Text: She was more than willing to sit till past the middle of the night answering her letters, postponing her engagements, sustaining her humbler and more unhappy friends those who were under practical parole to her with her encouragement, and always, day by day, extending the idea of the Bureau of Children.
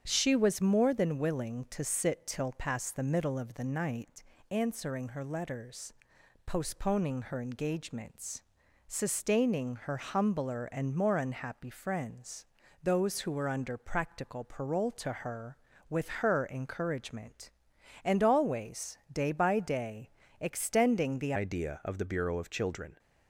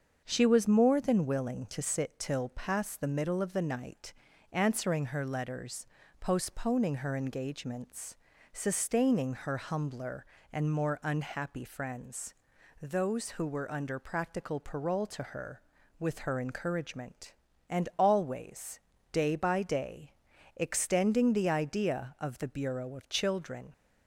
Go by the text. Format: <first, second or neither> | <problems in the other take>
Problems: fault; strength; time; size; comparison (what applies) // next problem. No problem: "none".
second | starts louder than the rest; strong; until 1.0 s; 8 dB; also in the second // pauses between "night" and "answering"; slight; at 4.2 s; 0.30 s long; also in the second // pauses between "friends" and "those"; at 12.4 s; 0.38 s long; noticeable in the second // changes voice at "idea"; from 21.3 s on; 1.6 s long